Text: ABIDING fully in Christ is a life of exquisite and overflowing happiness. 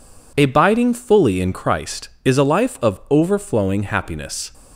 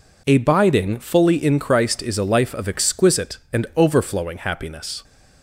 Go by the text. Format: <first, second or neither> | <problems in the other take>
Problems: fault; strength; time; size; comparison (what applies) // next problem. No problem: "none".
second | skips "exquisite and"; at 3.0 s